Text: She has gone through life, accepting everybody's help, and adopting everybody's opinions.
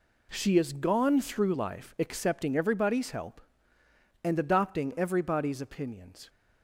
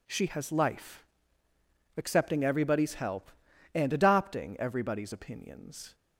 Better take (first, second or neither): first